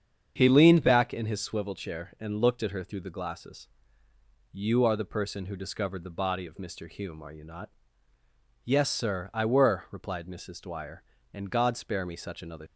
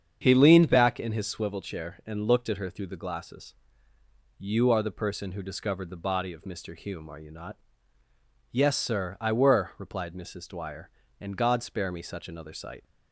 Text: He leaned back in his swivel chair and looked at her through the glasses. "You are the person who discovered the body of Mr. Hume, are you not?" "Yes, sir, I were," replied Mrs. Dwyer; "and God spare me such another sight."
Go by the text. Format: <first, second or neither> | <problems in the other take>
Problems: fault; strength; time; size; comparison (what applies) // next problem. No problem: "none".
second | starts louder than the rest; strong; until 1.3 s; 7.5 dB; strong in the second // stops before "sight"; at 12.6 s